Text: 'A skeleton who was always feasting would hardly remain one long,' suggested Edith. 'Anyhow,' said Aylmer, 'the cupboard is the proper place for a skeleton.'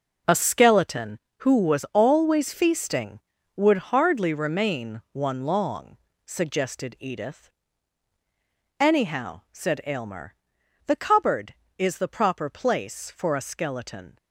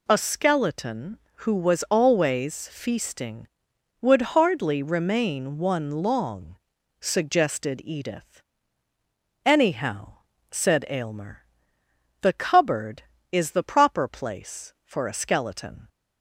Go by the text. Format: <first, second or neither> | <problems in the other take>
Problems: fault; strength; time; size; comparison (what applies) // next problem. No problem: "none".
second | gets quieter; strong; throughout; 10.5 dB